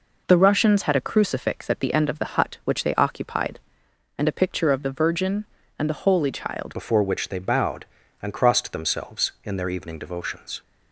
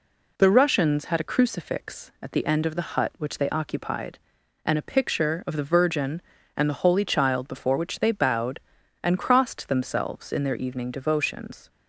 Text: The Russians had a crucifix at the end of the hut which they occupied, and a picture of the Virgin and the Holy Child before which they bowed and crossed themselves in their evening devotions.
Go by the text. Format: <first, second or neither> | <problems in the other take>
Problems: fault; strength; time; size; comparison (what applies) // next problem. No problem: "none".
second | changes voice at "before"; from 6.7 s on; 3.9 s long